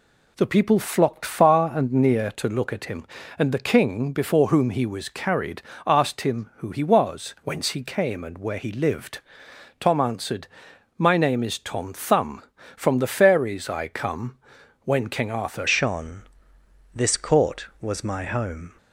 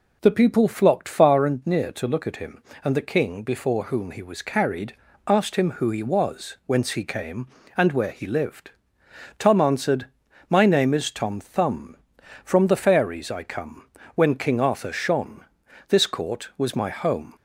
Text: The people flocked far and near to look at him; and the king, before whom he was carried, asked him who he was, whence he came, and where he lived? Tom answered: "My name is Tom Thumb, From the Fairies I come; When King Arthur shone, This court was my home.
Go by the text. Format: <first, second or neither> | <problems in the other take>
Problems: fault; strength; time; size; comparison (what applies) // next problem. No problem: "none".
second | changes voice at "shone"; from 15.6 s on; 3.1 s long